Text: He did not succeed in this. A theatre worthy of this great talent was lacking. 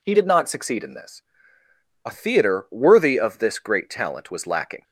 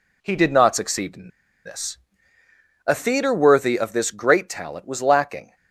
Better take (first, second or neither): first